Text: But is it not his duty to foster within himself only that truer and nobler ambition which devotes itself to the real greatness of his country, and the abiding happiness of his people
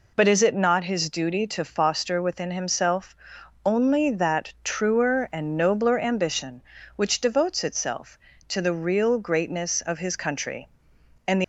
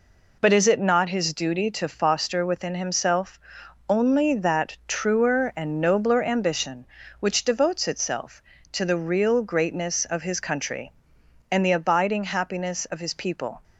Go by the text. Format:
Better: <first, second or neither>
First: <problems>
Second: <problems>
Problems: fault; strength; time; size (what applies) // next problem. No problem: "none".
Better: second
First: pauses between "himself" and "only"; noticeable; at 3.1 s; 0.50 s long // stops before "abiding happiness of his people"; at 11.4 s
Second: pauses between "himself" and "only"; noticeable; at 3.3 s; 0.50 s long